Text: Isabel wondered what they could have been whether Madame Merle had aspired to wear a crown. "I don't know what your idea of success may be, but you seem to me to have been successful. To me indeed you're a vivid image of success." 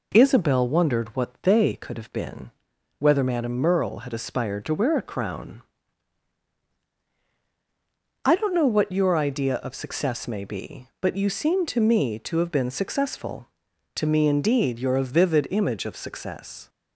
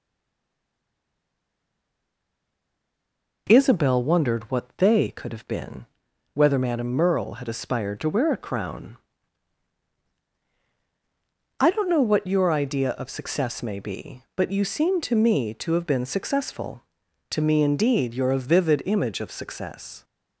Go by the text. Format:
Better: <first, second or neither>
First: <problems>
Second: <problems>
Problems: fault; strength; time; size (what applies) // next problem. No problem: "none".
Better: first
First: pauses between "been" and "whether"; noticeable; at 2.5 s; 0.48 s long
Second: stays silent before the first word; strong; until 3.4 s; 3.4 s long // pauses between "been" and "whether"; noticeable; at 5.8 s; 0.48 s long